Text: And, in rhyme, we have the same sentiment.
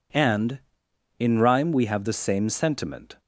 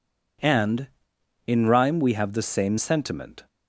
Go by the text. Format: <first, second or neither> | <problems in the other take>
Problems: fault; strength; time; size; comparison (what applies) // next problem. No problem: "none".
neither | none